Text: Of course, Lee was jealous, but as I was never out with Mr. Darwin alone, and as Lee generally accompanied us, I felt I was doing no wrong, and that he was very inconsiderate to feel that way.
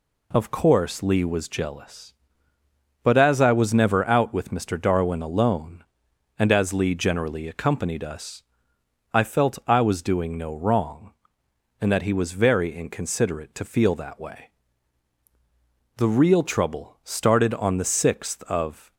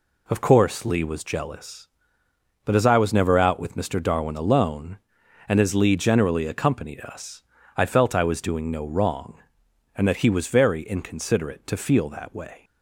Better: second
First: goes on to say "The real trouble started on the sixth of"; strong; from 15.9 s on; 2.9 s long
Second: none

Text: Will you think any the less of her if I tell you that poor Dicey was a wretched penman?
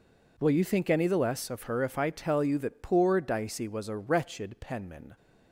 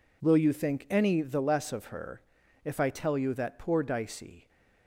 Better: first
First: none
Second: pauses between "her" and "if"; at 2.2 s; 0.42 s long // stops before "was a wretched penman"; at 4.4 s

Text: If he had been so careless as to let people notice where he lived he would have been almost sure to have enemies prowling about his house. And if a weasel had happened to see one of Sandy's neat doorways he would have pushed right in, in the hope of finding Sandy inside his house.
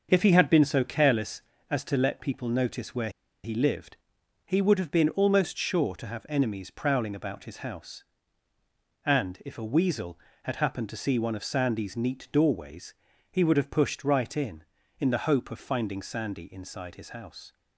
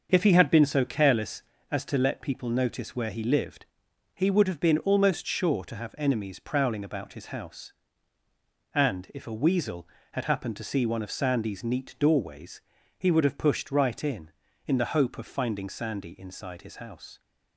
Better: second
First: starts louder than the rest; until 1.1 s; 6.5 dB // pauses between "where" and "he"; slight; at 3.0 s; 0.34 s long // pauses between "lived" and "he"; noticeable; at 3.9 s; 0.48 s long // pauses between "doorways" and "he"; slight; at 12.9 s; 0.36 s long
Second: starts louder than the rest; until 1.1 s; 6.5 dB // pauses between "lived" and "he"; noticeable; at 3.6 s; 0.48 s long // pauses between "doorways" and "he"; slight; at 12.6 s; 0.36 s long

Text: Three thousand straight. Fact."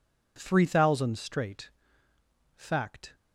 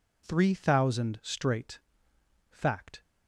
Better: neither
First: none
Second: none

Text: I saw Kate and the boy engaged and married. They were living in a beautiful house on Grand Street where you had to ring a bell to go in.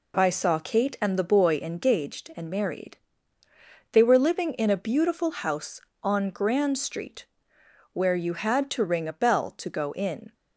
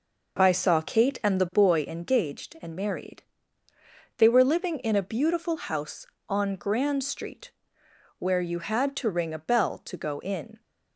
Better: first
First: pauses between "Street" and "where"; noticeable; at 7.2 s; 0.66 s long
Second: starts louder than the rest; noticeable; until 1.7 s; 5.5 dB // pauses between "Street" and "where"; noticeable; at 7.5 s; 0.66 s long

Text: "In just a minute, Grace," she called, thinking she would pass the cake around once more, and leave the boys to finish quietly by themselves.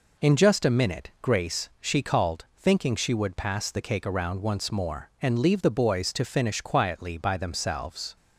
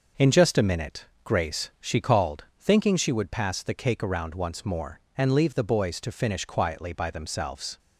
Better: neither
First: none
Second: none

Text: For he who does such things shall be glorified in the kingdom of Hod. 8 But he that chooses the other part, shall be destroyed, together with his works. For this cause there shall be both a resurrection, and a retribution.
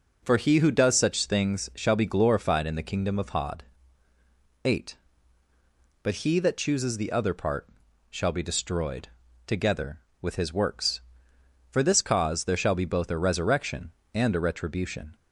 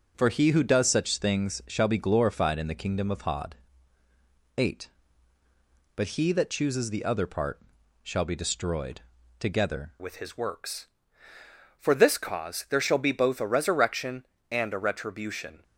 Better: first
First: none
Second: changes voice at "with"; from 9.9 s on; 5.7 s long

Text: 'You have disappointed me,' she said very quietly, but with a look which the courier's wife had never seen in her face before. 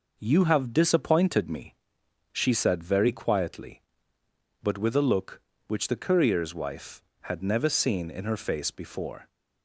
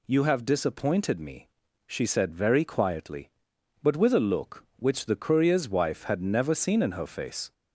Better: first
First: none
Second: stops before "before"; at 7.5 s

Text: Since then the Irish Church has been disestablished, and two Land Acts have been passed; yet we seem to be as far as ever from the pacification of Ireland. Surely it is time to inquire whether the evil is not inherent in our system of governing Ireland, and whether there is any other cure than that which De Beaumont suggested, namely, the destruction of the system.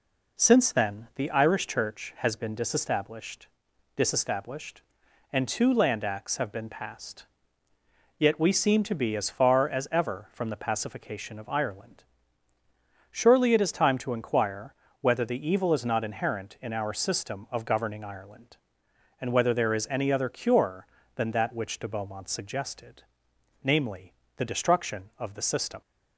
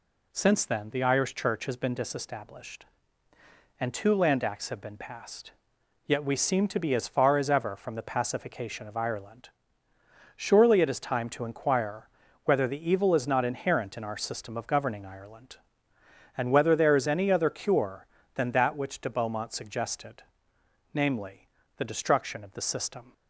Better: second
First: says "disestablished" twice; at 3.9 s // pauses between "inquire" and "whether"; slight; at 14.7 s; 0.26 s long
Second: pauses between "inquire" and "whether"; slight; at 12.0 s; 0.36 s long

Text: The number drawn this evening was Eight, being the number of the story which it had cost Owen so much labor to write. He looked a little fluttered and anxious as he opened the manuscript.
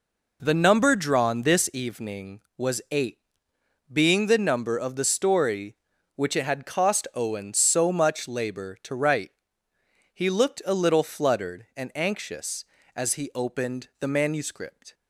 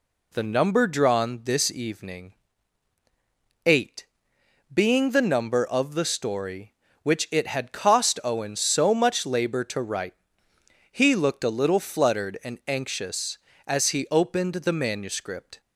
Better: first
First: none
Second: skips "was"; at 2.9 s

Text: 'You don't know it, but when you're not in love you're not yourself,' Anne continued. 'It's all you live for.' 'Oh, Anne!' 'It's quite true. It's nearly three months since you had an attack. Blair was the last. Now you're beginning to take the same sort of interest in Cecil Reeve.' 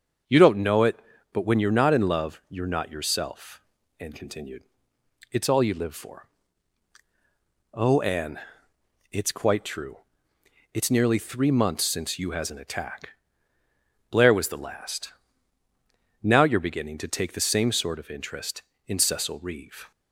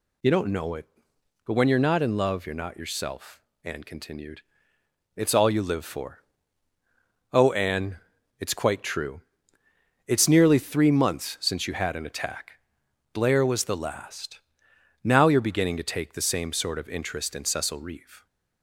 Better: second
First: starts louder than the rest; until 1.6 s; 7 dB // says "has" for "had"; at 12.3 s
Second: none

